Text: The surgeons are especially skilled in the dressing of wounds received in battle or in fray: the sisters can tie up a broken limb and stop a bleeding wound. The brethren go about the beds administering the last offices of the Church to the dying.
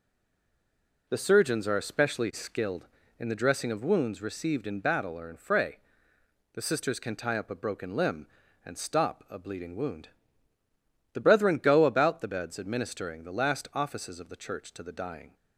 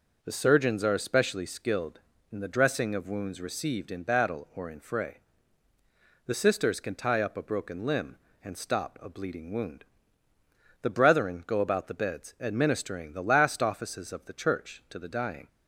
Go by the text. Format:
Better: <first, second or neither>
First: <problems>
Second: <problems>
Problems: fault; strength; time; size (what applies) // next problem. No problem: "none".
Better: second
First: stays silent before the first word; until 1.0 s; 1.0 s long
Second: none